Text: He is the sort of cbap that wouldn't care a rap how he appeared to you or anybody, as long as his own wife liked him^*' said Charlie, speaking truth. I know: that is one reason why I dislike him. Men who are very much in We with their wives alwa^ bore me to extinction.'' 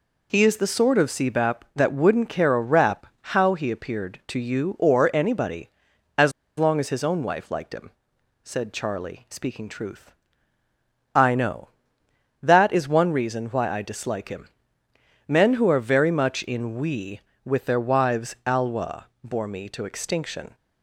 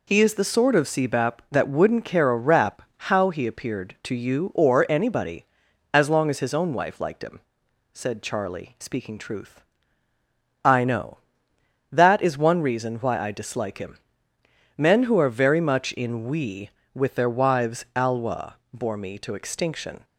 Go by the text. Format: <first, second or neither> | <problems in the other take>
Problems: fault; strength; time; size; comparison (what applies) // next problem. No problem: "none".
second | pauses between "rap" and "how"; slight; at 3.0 s; 0.30 s long; slight in the second // pauses between "as" and "long"; slight; at 6.3 s; 0.26 s long // pauses between "him" and "said"; noticeable; at 7.9 s; 0.52 s long; noticeable in the second